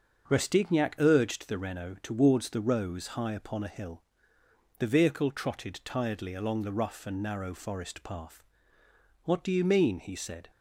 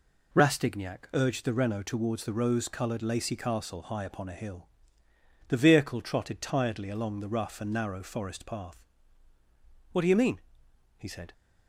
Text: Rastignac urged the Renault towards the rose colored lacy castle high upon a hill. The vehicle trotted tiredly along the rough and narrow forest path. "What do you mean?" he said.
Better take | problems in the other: second | starts louder than the rest; until 1.3 s; 6.5 dB // skips "colored lacy castle"; at 3.0 s

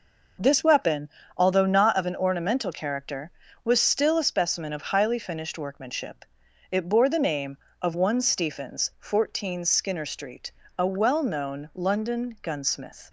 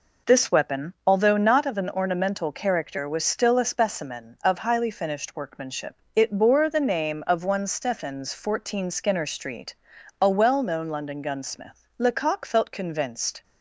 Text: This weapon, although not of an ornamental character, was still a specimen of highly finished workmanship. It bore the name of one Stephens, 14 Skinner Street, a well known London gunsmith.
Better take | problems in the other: first | goes on to say "Lecoq felt convinced"; from 11.9 s on; 1.4 s long

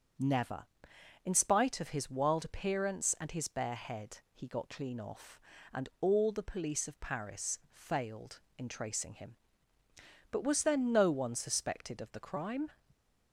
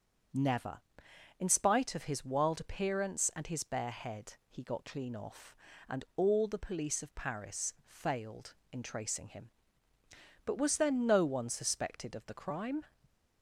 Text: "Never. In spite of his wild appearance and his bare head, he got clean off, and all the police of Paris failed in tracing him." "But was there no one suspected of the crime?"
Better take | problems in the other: neither | starts louder than the rest; the same in both

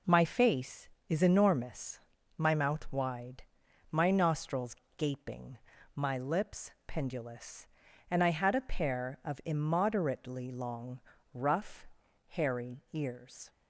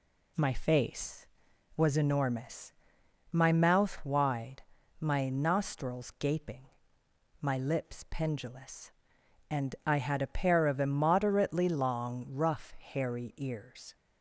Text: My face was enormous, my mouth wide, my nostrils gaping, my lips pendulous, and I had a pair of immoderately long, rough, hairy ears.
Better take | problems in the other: second | says "is" for "was"; at 1.0 s // pauses between "nostrils" and "gaping"; slight; at 4.7 s; 0.22 s long // pauses between "lips" and "pendulous"; slight; at 6.6 s; 0.16 s long

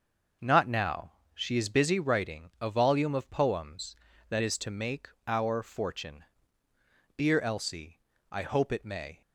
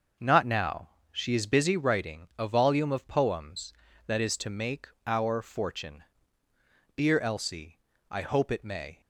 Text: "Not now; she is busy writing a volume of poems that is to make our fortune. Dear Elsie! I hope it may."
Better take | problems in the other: neither | starts louder than the rest; noticeable; the same in both // pauses between "make" and "our"; slight; the same in both

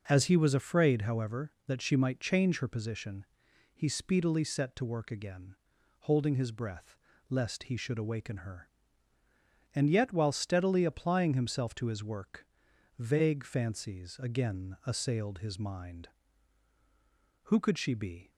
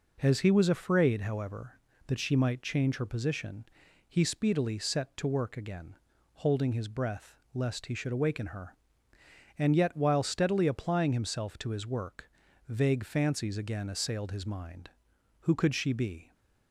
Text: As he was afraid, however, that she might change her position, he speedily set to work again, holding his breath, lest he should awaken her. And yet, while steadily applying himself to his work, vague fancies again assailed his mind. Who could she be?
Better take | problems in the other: neither | none

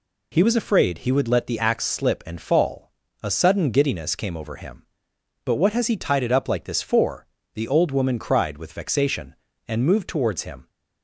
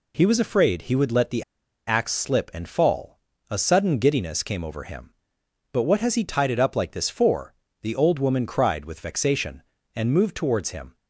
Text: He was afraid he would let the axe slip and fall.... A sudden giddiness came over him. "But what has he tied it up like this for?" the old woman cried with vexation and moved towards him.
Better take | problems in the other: first | pauses between "the" and "axe"; at 1.4 s; 0.43 s long

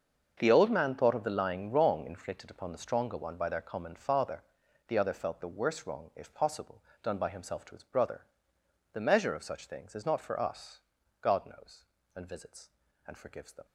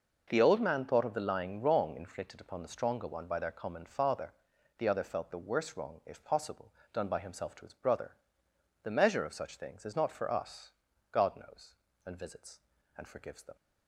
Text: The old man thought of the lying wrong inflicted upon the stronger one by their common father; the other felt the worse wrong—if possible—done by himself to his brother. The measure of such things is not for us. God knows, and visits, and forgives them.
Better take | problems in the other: second | gets quieter; strong; throughout; 14.5 dB

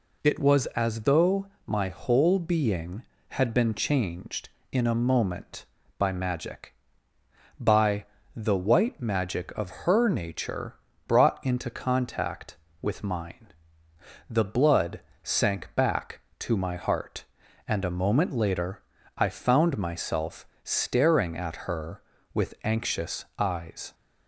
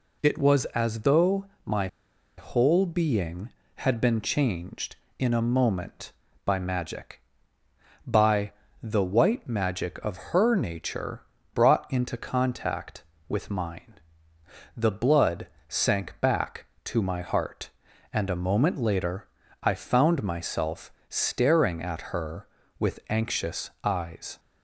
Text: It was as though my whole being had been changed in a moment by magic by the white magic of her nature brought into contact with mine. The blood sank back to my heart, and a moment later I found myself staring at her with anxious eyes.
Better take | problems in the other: first | pauses between "though" and "my"; slight; at 1.4 s; 0.20 s long; slight in the first // pauses between "my" and "whole"; noticeable; at 1.8 s; 0.50 s long // pauses between "by" and "the"; slight; at 8.5 s; 0.28 s long; slight in the first // pauses between "nature" and "brought"; slight; at 11.2 s; 0.30 s long; slight in the first // pauses between "blood" and "sank"; slight; at 15.4 s; 0.20 s long; slight in the first // pauses between "later" and "I"; slight; at 19.2 s; 0.34 s long; slight in the first // pauses between "myself" and "staring"; slight; at 20.8 s; 0.20 s long; slight in the first

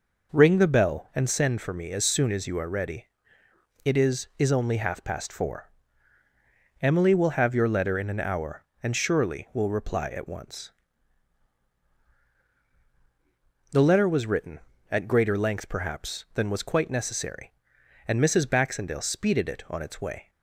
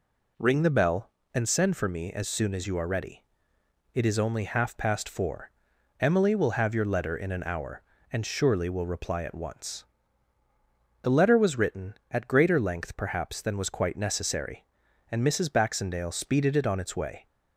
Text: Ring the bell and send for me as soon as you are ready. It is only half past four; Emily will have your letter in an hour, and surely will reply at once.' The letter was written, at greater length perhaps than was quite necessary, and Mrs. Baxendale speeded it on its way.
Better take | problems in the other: second | says "is" twice; at 4.3 s

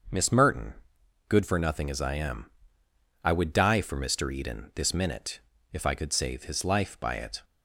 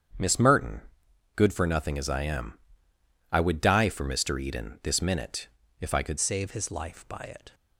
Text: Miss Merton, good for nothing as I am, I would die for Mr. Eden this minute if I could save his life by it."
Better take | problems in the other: first | starts louder than the rest; strong; until 1.7 s; 8 dB; also in the first // pauses between "minute" and "if"; slight; at 5.4 s; 0.32 s long; slight in the first // changes voice at "save"; from 6.1 s on; 1.4 s long

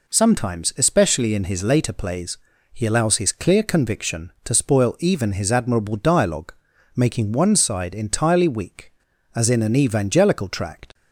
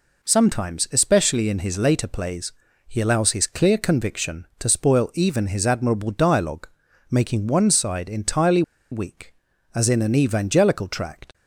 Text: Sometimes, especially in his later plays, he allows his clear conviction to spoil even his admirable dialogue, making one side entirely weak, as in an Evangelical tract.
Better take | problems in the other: first | pauses between "entirely" and "weak"; slight; at 8.6 s; 0.29 s long

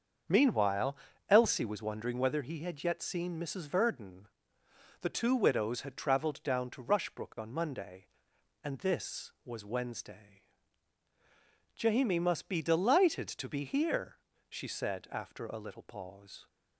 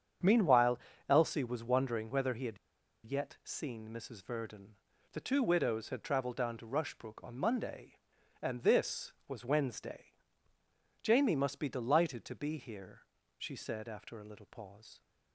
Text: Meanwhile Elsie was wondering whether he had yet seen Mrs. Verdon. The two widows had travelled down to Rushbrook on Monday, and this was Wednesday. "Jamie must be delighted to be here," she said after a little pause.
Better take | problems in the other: first | starts louder than the rest; strong; until 1.5 s; 8 dB; also in the first // pauses between "Meanwhile" and "Elsie"; slight; at 0.7 s; 0.32 s long; slight in the first // pauses between "had" and "yet"; noticeable; at 2.5 s; 0.49 s long

